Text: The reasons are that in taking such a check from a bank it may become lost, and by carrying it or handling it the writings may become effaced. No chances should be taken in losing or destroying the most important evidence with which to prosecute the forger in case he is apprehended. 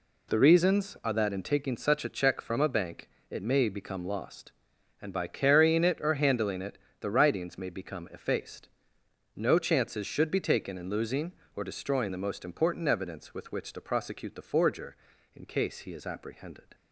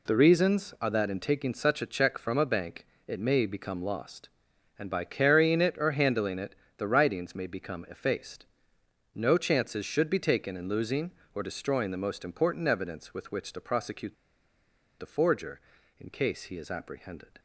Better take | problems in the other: first | pauses between "bank" and "it"; slight; at 2.8 s; 0.22 s long; slight in the first // pauses between "it" and "the"; slight; at 6.5 s; 0.22 s long; slight in the first // pauses between "prosecute" and "the"; noticeable; at 14.1 s; 0.85 s long

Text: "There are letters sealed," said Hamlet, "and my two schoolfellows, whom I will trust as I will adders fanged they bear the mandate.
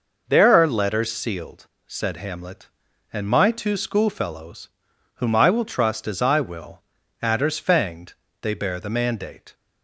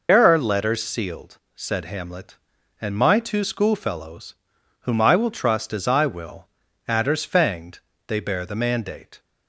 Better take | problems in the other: first | loses the start of "There"; at 0.0 s; 110 ms // pauses between "will" and "adders"; at 6.4 s; 0.40 s long; also in the first // pauses between "fanged" and "they"; slight; at 7.7 s; 0.30 s long; slight in the first

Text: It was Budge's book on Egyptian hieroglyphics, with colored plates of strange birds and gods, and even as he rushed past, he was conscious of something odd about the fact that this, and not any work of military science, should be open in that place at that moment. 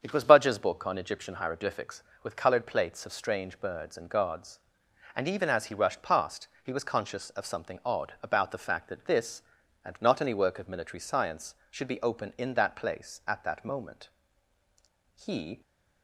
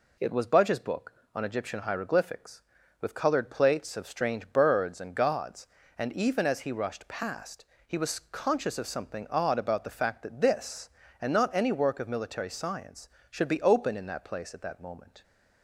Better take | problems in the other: second | starts louder than the rest; strong; until 1.0 s; 7.5 dB // goes on to say "He"; slight; from 15.1 s on; 0.46 s long

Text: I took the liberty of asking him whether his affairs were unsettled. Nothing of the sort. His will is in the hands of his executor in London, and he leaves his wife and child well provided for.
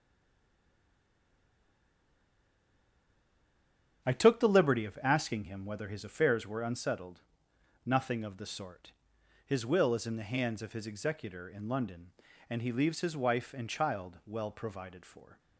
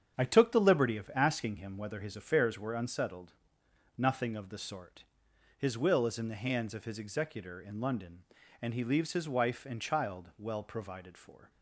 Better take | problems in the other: second | stays silent before the first word; strong; until 4.0 s; 4.0 s long // starts louder than the rest; strong; until 5.0 s; 8 dB; strong in the second

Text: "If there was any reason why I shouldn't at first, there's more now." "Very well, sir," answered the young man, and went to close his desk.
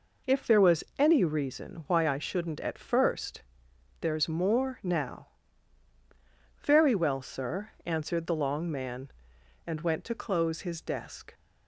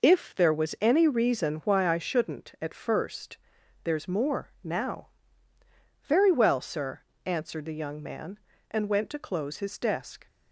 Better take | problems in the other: second | says "long" for "young"; at 8.3 s

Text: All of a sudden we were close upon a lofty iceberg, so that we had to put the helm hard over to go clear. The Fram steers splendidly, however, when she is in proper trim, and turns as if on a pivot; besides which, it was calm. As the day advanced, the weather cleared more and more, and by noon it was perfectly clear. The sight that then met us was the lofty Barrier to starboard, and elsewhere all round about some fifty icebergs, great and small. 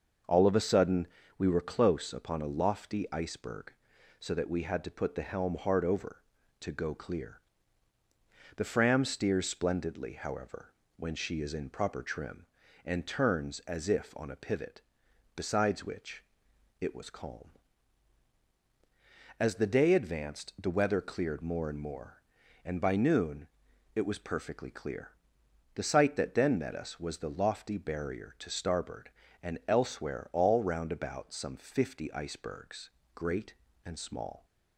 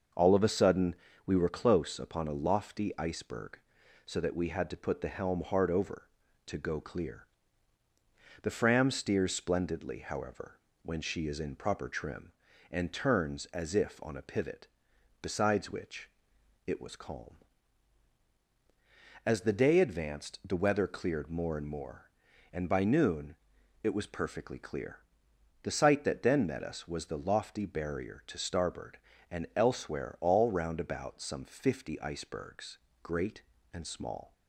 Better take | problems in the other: neither | starts louder than the rest; the same in both // pauses between "sudden" and "we"; slight; the same in both // pauses between "noon" and "it"; noticeable; the same in both

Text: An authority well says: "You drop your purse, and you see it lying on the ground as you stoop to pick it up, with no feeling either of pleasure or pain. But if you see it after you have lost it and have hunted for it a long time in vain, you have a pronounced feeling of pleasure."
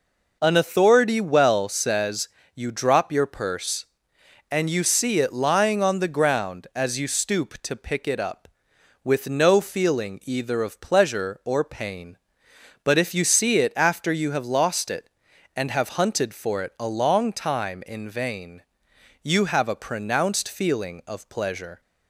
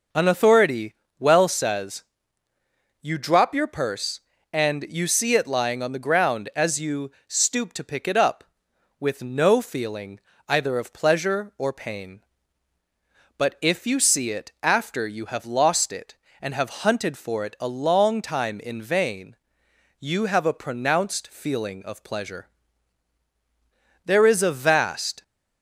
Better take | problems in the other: first | pauses between "authority" and "well"; slight; at 0.9 s; 0.26 s long // pauses between "you" and "stoop"; slight; at 7.1 s; 0.16 s long // pauses between "feeling" and "either"; slight; at 10.1 s; 0.30 s long // goes on to say "There is a vast"; noticeable; from 24.0 s on; 1.1 s long

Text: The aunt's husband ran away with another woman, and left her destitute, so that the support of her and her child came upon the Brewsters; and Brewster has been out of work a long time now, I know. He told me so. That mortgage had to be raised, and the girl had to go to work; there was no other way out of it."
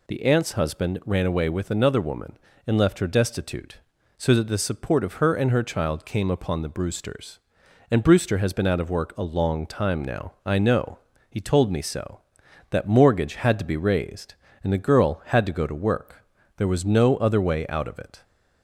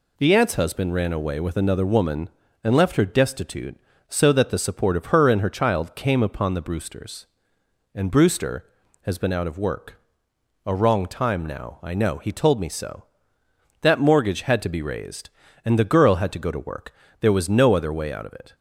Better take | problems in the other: first | pauses between "work" and "a"; noticeable; at 9.9 s; 0.66 s long // says "wrong" for "long"; at 10.7 s

